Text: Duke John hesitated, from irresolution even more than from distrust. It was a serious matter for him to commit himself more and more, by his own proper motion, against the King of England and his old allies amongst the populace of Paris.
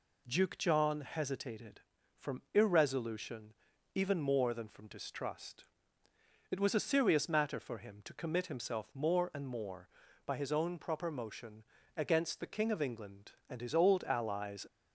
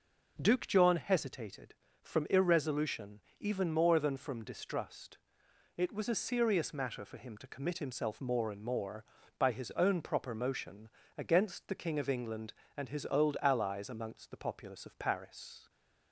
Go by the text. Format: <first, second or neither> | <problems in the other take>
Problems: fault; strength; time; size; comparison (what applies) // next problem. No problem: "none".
second | pauses between "irresolution" and "even"; at 3.5 s; 0.42 s long; slight in the second // stops before "amongst the populace of Paris"; at 14.6 s